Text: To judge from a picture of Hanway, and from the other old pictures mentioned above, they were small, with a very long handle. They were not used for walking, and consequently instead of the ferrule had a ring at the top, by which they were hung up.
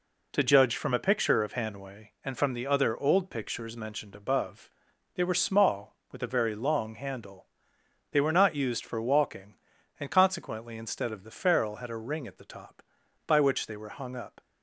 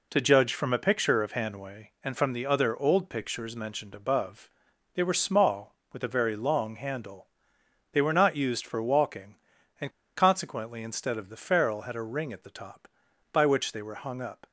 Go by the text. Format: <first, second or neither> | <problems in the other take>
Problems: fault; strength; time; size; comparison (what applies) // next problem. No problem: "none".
first | pauses between "and" and "consequently"; slight; at 9.9 s; 0.25 s long